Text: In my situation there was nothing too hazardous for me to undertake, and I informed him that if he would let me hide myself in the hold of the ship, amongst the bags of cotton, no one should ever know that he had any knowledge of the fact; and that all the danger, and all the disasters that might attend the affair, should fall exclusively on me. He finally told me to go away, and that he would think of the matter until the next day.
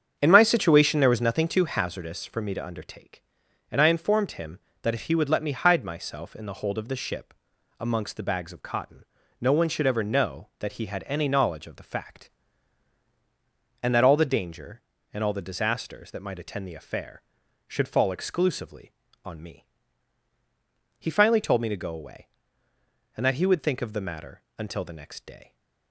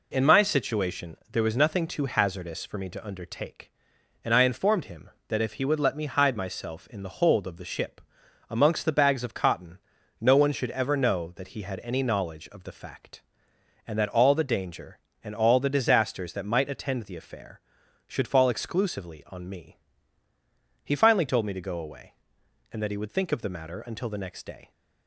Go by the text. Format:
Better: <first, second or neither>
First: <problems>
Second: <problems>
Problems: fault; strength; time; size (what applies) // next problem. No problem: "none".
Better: second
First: starts louder than the rest; strong; until 1.9 s; 7.5 dB // pauses between "matter" and "until"; slight; at 24.3 s; 0.18 s long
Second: none